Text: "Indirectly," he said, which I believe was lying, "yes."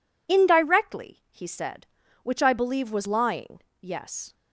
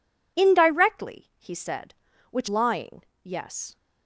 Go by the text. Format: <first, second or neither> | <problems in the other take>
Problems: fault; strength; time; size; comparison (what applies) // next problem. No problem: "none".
first | skips "I believe was"; at 2.4 s